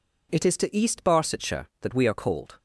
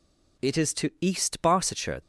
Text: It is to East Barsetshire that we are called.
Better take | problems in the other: first | stops before "that we are called"; at 2.0 s

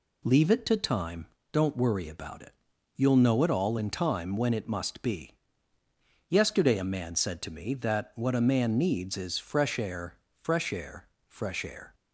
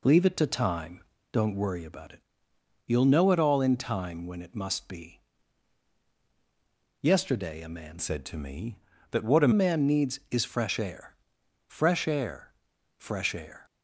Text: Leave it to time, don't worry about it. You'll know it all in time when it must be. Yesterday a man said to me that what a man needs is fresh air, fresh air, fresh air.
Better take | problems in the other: first | changes voice from "said" to "a"; from 7.9 to 9.5 s; 1.6 s long

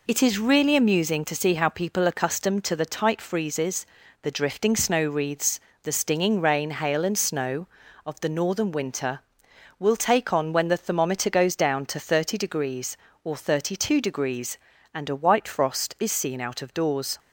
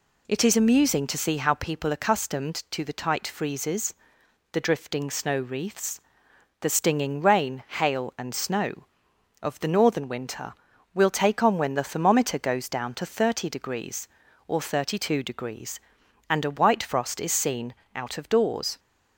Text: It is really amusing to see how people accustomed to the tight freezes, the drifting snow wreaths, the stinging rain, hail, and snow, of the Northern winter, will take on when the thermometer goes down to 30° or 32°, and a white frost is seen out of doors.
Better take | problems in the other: first | skips "really"; at 0.5 s // pauses between "seen" and "out"; slight; at 17.7 s; 0.20 s long

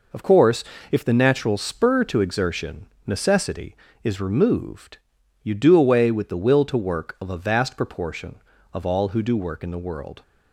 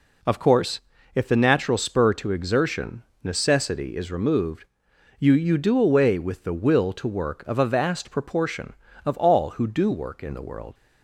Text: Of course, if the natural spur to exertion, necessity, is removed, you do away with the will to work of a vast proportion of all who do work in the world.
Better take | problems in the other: first | says "you" twice; at 5.3 s

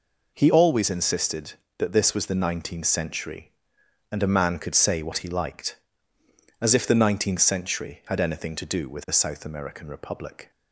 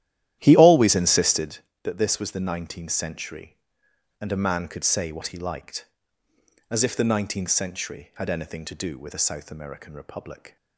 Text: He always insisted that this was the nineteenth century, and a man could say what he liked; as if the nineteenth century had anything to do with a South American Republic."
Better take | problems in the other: first | starts louder than the rest; strong; until 1.6 s; 12.5 dB

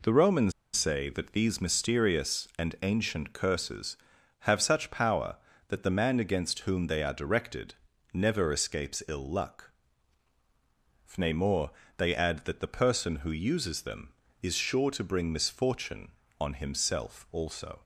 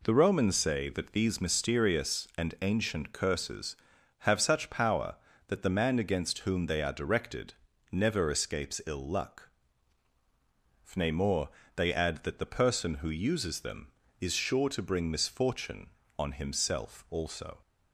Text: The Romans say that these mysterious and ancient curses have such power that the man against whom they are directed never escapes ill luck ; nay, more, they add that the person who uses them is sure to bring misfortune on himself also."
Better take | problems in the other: second | pauses between "Romans" and "say"; slight; at 0.5 s; 0.24 s long // pauses between "directed" and "never"; at 7.7 s; 0.38 s long; also in the second

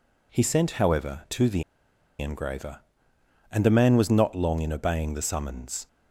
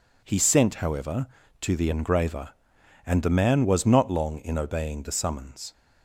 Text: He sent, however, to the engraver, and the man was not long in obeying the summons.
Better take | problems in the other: second | pauses between "the" and "engraver"; noticeable; at 1.6 s; 0.56 s long

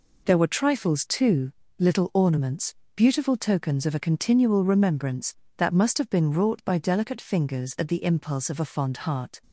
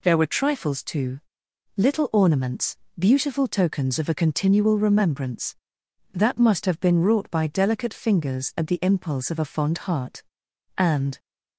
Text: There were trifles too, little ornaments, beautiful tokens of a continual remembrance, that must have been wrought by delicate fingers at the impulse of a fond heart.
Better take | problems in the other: first | goes on to say "And"; slight; from 10.7 s on; 0.42 s long

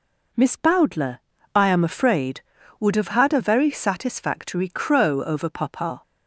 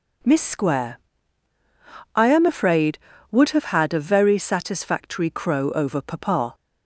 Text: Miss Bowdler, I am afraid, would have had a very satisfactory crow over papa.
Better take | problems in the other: first | says "Square" for "Bowdler"; at 0.4 s

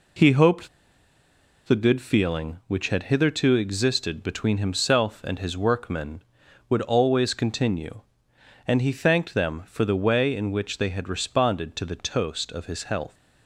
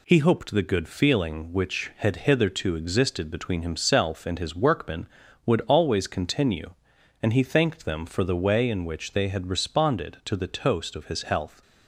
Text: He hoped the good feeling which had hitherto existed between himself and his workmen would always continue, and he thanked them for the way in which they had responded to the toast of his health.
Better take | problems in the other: second | pauses between "hoped" and "the"; at 0.6 s; 0.98 s long

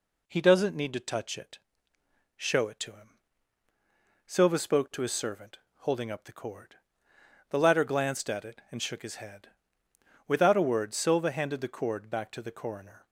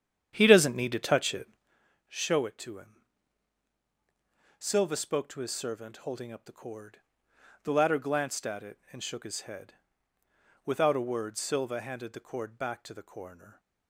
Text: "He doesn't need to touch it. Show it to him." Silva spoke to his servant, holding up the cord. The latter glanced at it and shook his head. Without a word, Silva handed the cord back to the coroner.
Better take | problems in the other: first | starts louder than the rest; strong; until 1.8 s; 9 dB

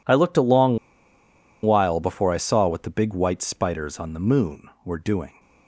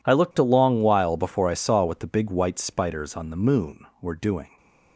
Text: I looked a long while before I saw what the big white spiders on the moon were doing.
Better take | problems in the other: second | pauses between "long" and "while"; noticeable; at 0.7 s; 0.87 s long

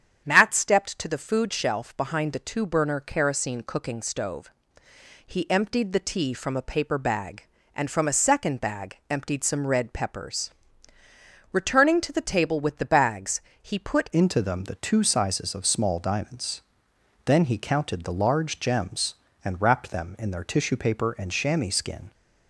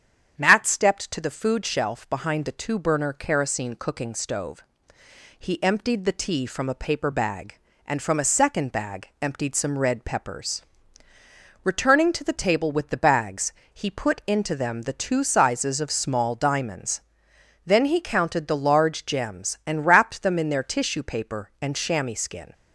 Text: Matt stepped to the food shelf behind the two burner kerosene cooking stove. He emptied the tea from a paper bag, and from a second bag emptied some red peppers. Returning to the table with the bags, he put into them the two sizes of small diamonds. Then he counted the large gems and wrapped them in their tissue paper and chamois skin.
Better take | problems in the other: second | starts louder than the rest; strong; until 1.2 s; 8.5 dB; strong in the second // changes voice at "into"; from 14.1 s on; 8.0 s long

